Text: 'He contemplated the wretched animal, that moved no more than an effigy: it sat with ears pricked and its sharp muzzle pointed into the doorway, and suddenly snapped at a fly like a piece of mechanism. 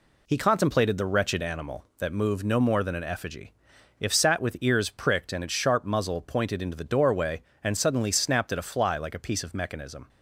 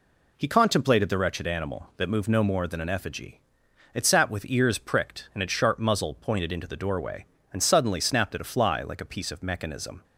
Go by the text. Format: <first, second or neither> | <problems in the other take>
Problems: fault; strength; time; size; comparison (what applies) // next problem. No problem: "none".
second | says "if" for "it"; at 4.0 s